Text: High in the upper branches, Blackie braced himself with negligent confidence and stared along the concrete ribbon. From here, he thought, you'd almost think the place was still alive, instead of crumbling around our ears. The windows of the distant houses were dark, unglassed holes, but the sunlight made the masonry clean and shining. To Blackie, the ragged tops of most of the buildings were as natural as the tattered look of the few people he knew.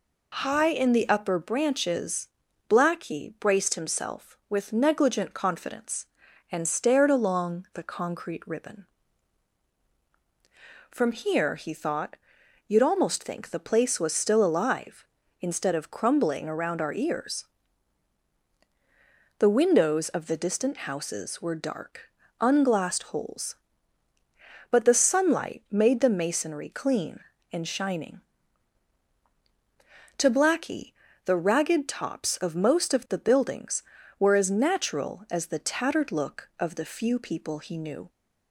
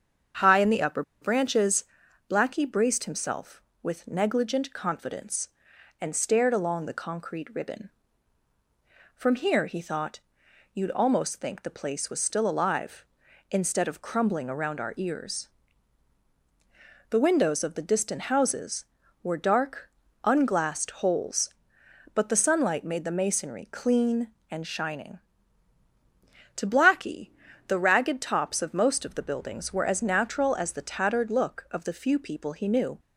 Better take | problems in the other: first | starts louder than the rest; strong; until 1.6 s; 7.5 dB // pauses between "upper" and "branches"; slight; at 1.0 s; 0.19 s long

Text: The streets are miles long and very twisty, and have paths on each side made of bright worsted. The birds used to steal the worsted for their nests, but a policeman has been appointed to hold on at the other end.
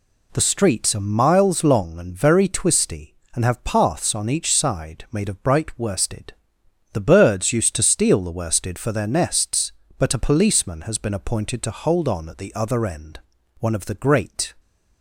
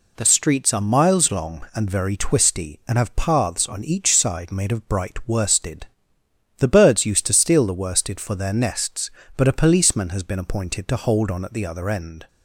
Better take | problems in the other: second | goes on to say "One of the great"; noticeable; from 13.5 s on; 0.94 s long

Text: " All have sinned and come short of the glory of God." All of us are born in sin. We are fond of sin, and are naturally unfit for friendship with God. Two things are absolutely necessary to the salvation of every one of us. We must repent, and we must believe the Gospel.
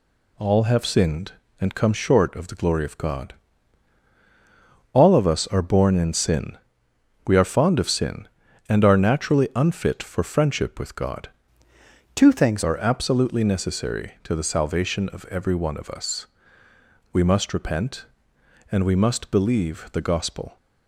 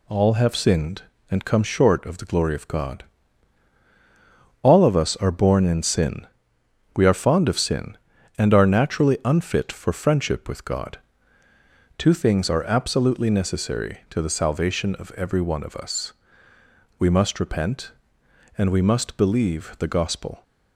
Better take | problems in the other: second | changes voice from "Two" to "things"; from 12.1 to 12.6 s; 0.5 s long

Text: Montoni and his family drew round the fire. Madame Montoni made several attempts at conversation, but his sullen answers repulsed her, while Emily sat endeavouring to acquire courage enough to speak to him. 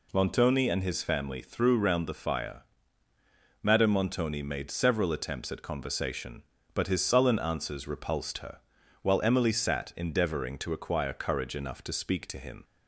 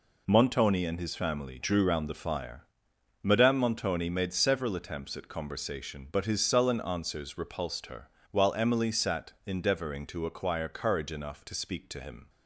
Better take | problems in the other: second | says "threw" for "drew"; at 1.3 s

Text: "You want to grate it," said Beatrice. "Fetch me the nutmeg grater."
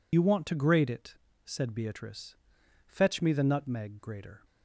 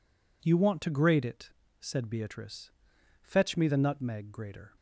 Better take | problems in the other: second | loses the start of "You"; at 0.1 s; 60 ms

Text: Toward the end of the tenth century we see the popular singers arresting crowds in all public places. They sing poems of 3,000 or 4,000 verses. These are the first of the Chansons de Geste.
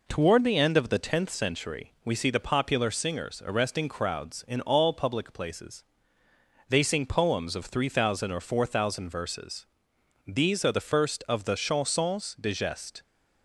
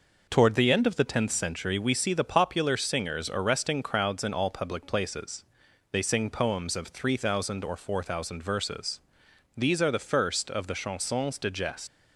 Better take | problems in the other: first | leaves "Geste" unfinished; at 11.8 s; 125 ms

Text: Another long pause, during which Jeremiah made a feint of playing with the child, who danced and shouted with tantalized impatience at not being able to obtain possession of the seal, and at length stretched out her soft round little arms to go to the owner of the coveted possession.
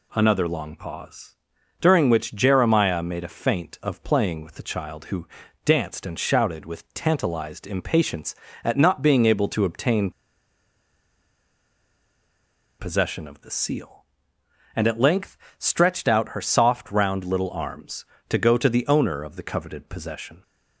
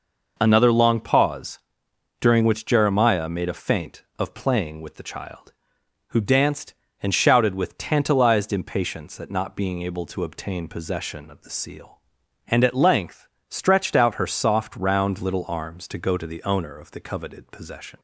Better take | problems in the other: second | pauses between "who" and "danced"; at 5.2 s; 0.38 s long // pauses between "obtain" and "possession"; strong; at 10.0 s; 2.6 s long // pauses between "length" and "stretched"; slight; at 15.3 s; 0.20 s long; slight in the second

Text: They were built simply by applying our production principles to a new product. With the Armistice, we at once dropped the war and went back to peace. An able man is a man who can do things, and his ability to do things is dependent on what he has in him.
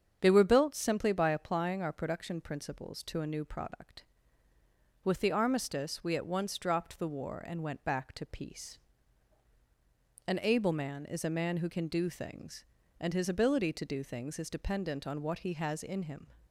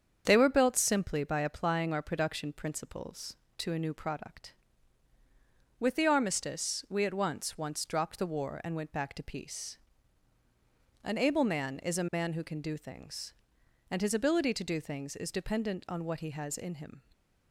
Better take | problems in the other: first | starts louder than the rest; strong; until 1.2 s; 7.5 dB; strong in the first // says "once" twice; at 7.5 s

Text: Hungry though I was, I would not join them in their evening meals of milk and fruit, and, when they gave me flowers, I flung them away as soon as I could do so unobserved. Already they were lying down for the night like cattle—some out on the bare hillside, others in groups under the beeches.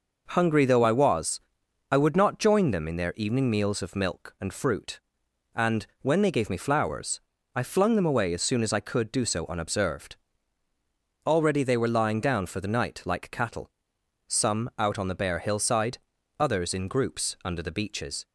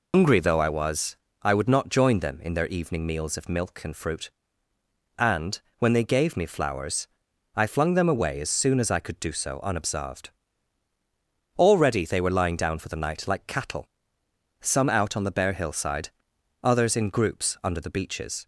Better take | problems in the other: first | loses the start of "Hungry"; at 0.1 s; 160 ms

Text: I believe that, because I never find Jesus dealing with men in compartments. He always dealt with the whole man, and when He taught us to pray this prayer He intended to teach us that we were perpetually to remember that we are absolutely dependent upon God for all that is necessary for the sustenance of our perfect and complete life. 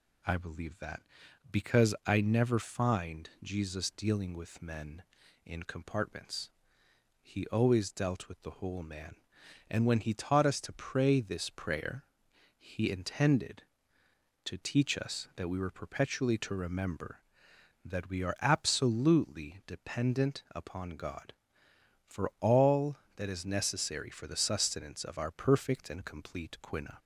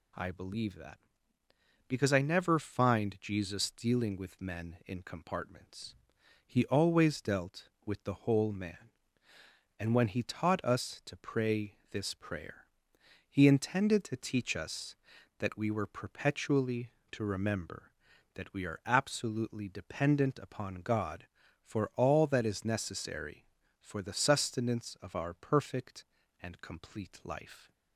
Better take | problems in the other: second | pauses between "prayer" and "He"; noticeable; at 12.0 s; 0.54 s long; noticeable in the second // says "quina" for "life"; at 26.6 s

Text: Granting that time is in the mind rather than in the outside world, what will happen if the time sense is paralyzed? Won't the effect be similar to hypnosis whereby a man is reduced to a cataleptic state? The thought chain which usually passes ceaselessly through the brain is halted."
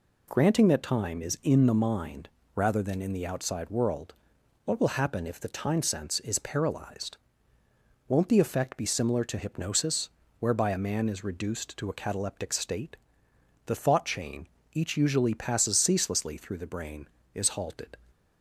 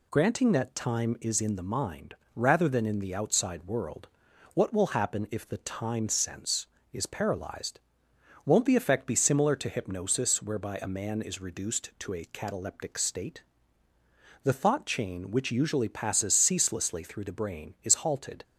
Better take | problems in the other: second | pauses between "mind" and "rather"; slight; at 2.2 s; 0.26 s long; slight in the second // pauses between "hypnosis" and "whereby"; slight; at 10.0 s; 0.30 s long // says "each" for "which"; at 14.7 s

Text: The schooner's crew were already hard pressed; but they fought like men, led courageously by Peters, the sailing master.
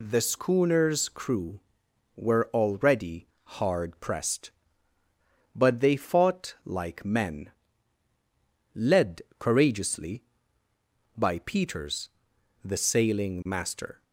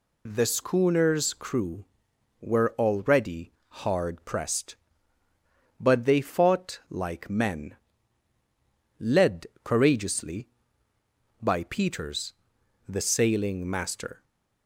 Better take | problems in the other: neither | pauses between "already" and "hard"; slight; the same in both // pauses between "led" and "courageously"; slight; the same in both

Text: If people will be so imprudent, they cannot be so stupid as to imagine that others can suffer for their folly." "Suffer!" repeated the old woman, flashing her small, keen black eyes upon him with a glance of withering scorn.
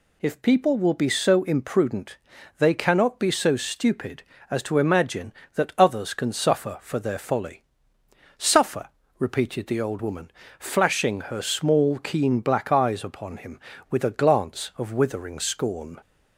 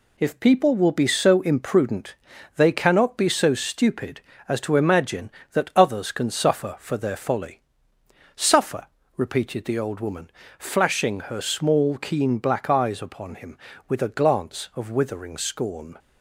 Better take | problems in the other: first | gets quieter; noticeable; throughout; 5.5 dB

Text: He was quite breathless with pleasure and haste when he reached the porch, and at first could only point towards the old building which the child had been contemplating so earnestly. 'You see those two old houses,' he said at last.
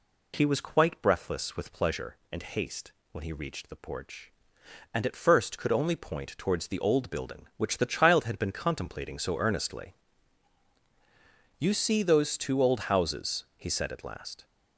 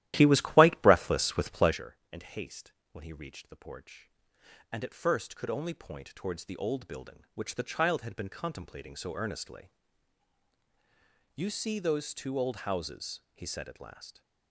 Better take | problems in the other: first | starts louder than the rest; strong; until 1.8 s; 13.5 dB // pauses between "haste" and "when"; slight; at 2.7 s; 0.22 s long; slight in the first

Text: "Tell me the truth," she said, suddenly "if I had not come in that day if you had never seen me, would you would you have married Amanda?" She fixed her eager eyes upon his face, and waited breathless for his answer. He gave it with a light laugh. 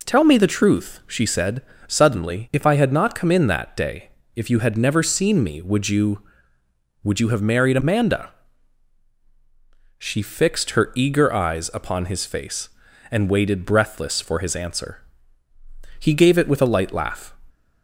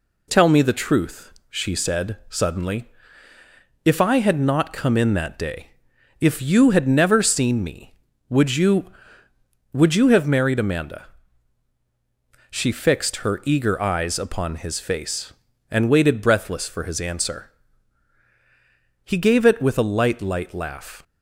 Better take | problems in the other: first | pauses between "suddenly" and "if"; noticeable; at 2.8 s; 0.96 s long // pauses between "day" and "if"; noticeable; at 5.7 s; 0.50 s long; slight in the first // says "light" twice; at 20.2 s

